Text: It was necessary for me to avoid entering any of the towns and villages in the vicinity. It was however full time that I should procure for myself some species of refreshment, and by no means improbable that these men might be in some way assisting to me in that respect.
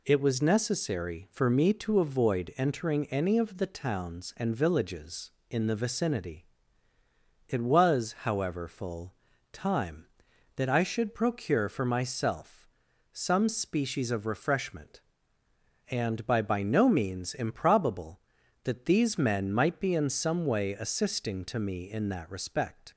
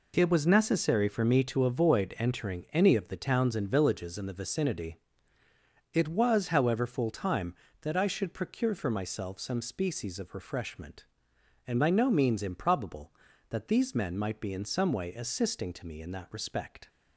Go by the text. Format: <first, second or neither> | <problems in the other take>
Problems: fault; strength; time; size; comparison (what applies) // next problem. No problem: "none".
second | pauses between "full" and "time"; at 9.1 s; 0.40 s long // pauses between "myself" and "some"; noticeable; at 12.6 s; 0.46 s long // says "by" twice; at 16.4 s